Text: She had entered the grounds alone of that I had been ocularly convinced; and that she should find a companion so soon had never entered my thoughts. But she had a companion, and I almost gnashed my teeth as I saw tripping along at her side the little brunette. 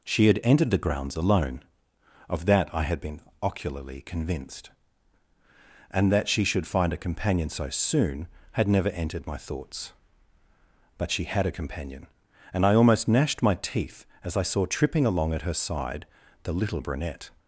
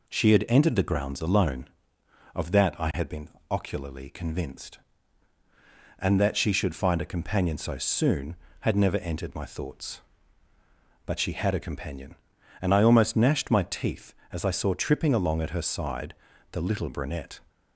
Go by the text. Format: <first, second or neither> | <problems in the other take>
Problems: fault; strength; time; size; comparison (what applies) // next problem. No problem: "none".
neither | pauses between "been" and "ocularly"; slight; the same in both // pauses between "side" and "the"; the same in both